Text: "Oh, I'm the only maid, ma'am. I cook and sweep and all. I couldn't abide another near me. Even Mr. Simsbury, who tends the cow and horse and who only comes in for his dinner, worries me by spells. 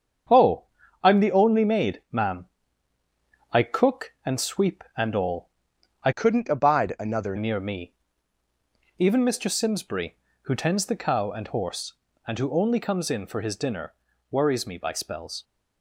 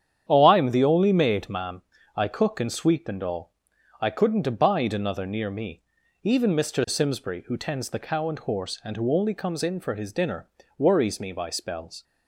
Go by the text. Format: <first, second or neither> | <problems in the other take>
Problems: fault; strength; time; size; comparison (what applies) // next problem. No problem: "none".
second | starts louder than the rest; strong; until 1.7 s; 7.5 dB; strong in the second // changes voice from "couldn't" to "another"; from 6.1 to 7.3 s; 1.2 s long